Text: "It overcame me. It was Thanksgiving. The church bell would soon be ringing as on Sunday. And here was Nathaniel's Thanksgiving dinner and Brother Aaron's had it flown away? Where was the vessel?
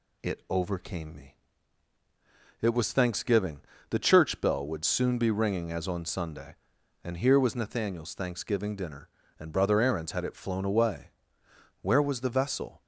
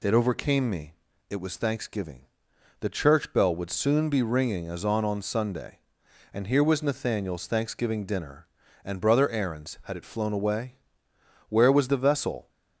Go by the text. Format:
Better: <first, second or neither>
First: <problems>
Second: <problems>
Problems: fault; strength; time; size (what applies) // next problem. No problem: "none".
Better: first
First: none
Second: says "on" twice; at 5.0 s